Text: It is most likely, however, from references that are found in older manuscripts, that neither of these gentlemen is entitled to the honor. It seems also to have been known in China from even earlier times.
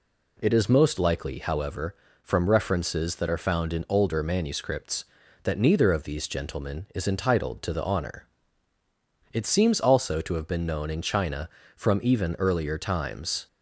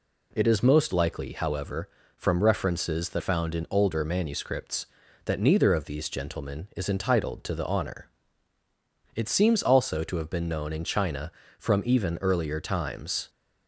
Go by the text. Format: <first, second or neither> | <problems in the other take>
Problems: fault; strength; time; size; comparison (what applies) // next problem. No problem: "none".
first | skips "are"; at 3.2 s